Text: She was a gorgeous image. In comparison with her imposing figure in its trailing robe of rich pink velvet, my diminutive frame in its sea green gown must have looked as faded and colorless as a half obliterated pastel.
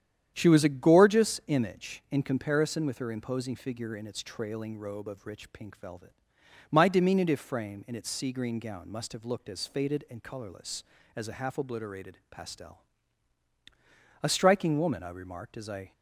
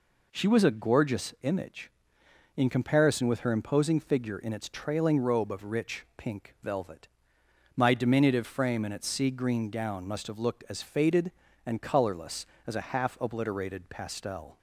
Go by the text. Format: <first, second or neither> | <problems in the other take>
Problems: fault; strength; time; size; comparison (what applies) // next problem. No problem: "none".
second | starts louder than the rest; strong; until 1.3 s; 9.5 dB // goes on to say "A striking woman I remarked as I"; strong; from 14.2 s on; 1.6 s long